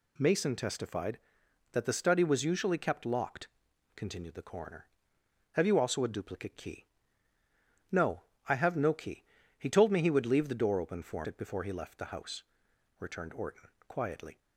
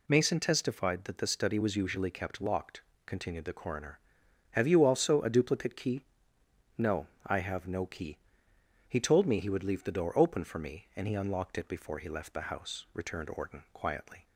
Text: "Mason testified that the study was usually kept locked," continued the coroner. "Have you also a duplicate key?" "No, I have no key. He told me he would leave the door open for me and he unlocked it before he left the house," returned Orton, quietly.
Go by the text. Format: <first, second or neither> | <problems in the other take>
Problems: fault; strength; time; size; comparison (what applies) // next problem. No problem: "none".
second | skips "me and he unlocked"; at 11.2 s